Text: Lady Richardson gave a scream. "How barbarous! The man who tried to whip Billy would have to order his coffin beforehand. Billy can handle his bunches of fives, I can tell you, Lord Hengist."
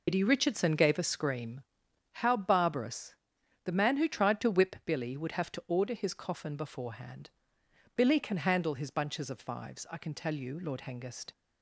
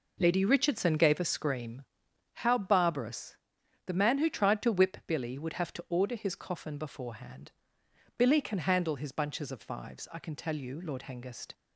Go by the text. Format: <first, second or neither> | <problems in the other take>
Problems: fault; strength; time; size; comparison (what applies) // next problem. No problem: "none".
second | loses the start of "Lady"; at 0.0 s; 110 ms